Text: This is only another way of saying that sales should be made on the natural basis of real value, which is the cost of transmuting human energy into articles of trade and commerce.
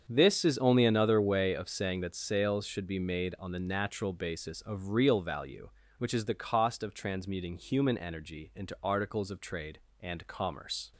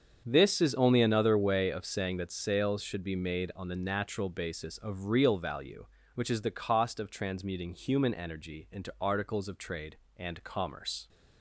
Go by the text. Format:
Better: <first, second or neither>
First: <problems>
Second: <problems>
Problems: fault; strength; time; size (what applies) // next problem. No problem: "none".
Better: neither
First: starts louder than the rest; strong; until 1.0 s; 7 dB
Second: starts louder than the rest; strong; until 1.2 s; 7.5 dB